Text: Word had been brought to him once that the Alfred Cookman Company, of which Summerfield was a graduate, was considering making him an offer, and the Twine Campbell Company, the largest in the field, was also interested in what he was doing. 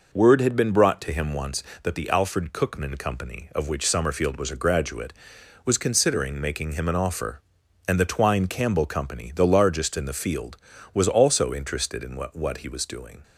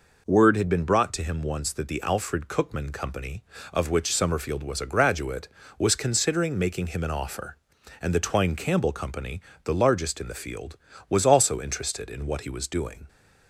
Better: second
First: says "what" twice; at 12.3 s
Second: none

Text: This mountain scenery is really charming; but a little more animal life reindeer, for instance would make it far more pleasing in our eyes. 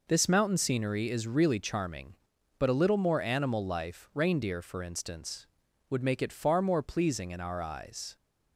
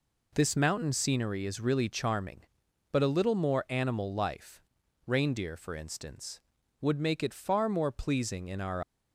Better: first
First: none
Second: pauses between "life" and "reindeer"; at 4.6 s; 0.44 s long // stops before "eyes"; at 8.8 s

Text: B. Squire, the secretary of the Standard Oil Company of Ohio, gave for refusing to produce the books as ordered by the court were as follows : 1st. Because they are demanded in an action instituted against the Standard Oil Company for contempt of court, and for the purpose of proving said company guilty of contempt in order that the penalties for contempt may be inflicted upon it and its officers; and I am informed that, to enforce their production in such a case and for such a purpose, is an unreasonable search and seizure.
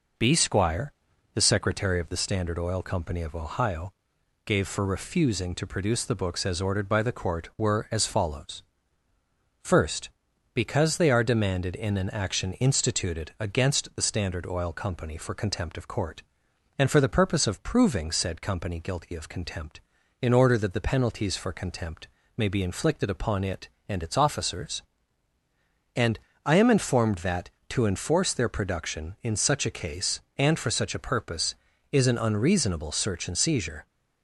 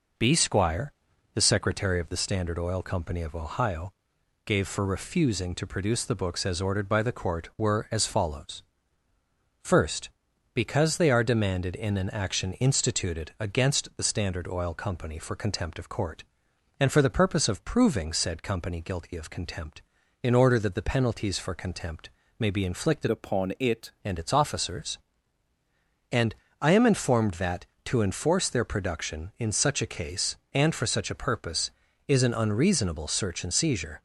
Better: first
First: pauses between "contempt" and "may"; slight; at 22.0 s; 0.30 s long // pauses between "and" and "I"; slight; at 26.1 s; 0.26 s long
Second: pauses between "contempt" and "may"; slight; at 22.0 s; 0.30 s long // changes voice from "upon" to "it"; from 23.0 to 23.9 s; 0.9 s long // pauses between "and" and "I"; slight; at 26.3 s; 0.26 s long

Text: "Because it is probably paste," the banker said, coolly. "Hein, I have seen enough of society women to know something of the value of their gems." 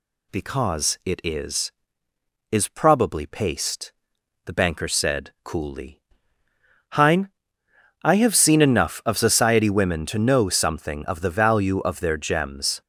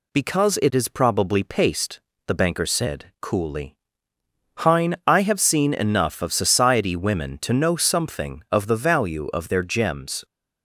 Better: second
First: says "is" twice; at 2.5 s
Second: none

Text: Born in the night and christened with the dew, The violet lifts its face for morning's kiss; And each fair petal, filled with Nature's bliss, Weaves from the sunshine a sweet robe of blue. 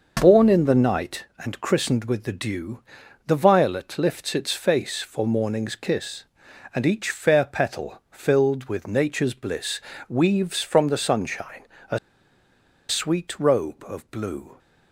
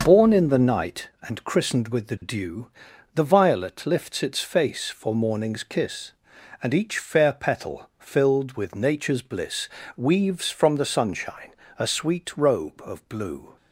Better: second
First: starts louder than the rest; noticeable; until 1.2 s; 6 dB // pauses between "sunshine" and "a"; slight; at 11.6 s; 0.26 s long // pauses between "a" and "sweet"; noticeable; at 11.9 s; 0.91 s long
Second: starts louder than the rest; noticeable; until 1.0 s; 6 dB // pauses between "sunshine" and "a"; slight; at 11.5 s; 0.26 s long

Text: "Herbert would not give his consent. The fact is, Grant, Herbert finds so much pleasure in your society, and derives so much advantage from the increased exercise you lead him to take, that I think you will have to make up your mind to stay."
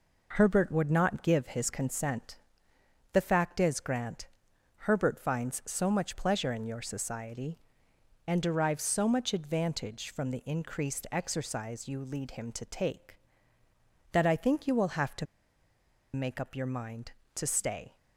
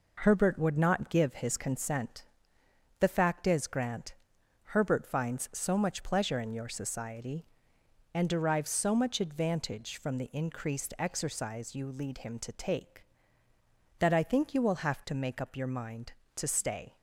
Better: second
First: pauses between "to" and "make"; noticeable; at 15.2 s; 0.88 s long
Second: none

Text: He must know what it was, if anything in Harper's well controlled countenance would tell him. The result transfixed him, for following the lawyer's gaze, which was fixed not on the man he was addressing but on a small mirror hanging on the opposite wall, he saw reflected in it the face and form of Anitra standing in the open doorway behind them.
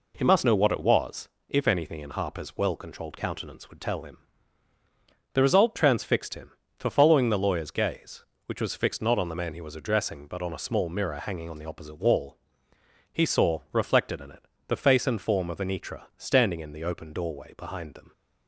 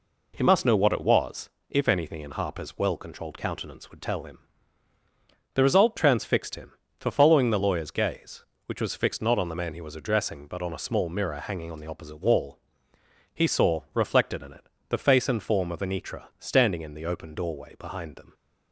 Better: neither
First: pauses between "it" and "the"; slight; at 14.4 s; 0.24 s long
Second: pauses between "it" and "the"; slight; at 14.6 s; 0.24 s long

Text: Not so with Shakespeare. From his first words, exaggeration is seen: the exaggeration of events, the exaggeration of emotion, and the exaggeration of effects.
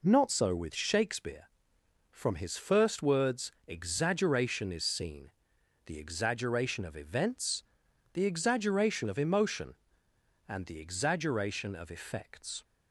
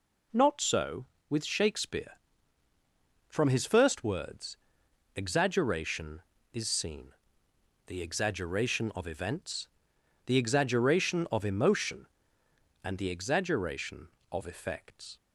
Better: neither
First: none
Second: none

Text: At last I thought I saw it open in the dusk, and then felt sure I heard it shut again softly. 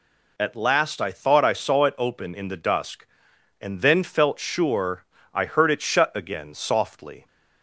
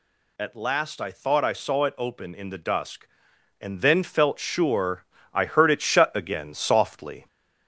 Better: first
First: pauses between "sure" and "I"; slight; at 5.0 s; 0.28 s long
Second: gets louder; slight; throughout; 2 dB // pauses between "sure" and "I"; slight; at 5.0 s; 0.28 s long

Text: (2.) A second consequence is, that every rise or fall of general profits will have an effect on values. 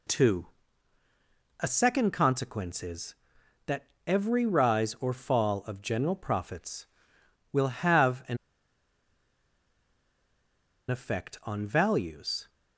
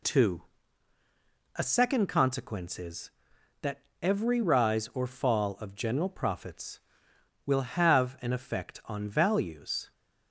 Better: second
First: pauses between "that" and "every"; slight; at 3.8 s; 0.22 s long // pauses between "an" and "effect"; strong; at 8.3 s; 2.5 s long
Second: pauses between "that" and "every"; slight; at 3.7 s; 0.22 s long

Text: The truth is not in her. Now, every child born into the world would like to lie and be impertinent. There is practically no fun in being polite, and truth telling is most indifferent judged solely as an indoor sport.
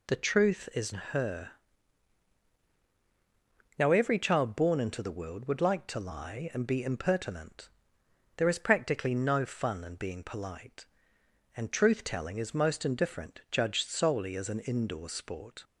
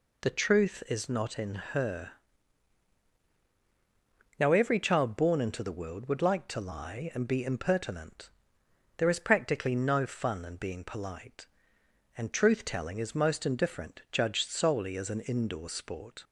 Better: second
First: skips "not in"; at 0.9 s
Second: none

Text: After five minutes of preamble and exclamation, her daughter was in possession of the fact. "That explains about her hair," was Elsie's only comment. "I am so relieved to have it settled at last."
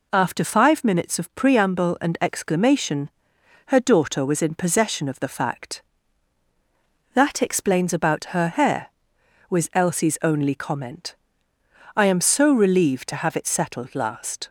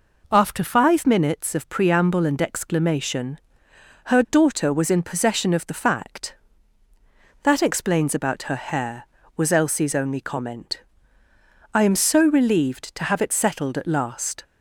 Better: second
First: skips "at"; at 13.9 s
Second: none

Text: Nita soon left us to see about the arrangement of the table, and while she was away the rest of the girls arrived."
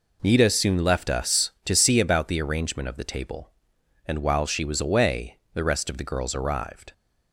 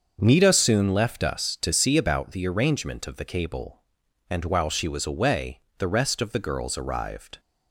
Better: first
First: pauses between "away" and "the"; slight; at 5.3 s; 0.18 s long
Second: starts louder than the rest; until 1.2 s; 6.5 dB // says "cable" for "table"; at 3.2 s // pauses between "away" and "the"; slight; at 5.6 s; 0.16 s long

